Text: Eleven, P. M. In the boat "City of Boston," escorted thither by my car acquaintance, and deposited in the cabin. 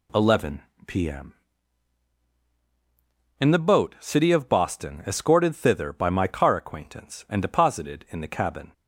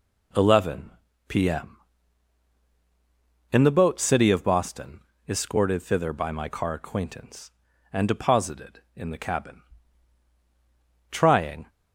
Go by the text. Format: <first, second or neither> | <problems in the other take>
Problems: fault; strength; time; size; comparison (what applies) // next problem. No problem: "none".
first | goes on to say "Trying"; from 11.0 s on; 0.60 s long